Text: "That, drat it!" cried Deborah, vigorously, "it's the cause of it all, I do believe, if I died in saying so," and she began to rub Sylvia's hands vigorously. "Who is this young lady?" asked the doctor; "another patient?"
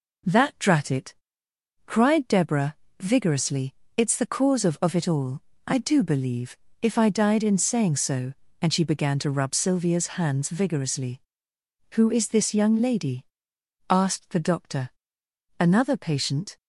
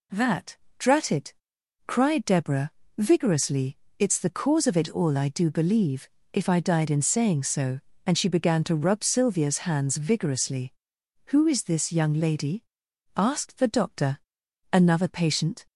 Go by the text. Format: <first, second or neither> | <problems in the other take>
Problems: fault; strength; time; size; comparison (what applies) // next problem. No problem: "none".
second | says "of" twice; at 4.8 s